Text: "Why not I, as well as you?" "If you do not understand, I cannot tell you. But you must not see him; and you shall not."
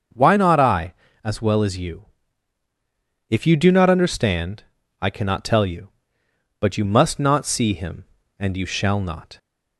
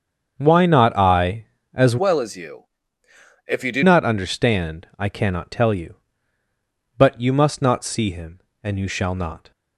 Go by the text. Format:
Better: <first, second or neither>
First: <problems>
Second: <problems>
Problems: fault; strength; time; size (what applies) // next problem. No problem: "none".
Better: first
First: starts louder than the rest; until 1.4 s; 6.5 dB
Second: starts louder than the rest; strong; until 1.3 s; 7 dB // changes voice from "well" to "do"; from 1.9 to 3.8 s; 1.9 s long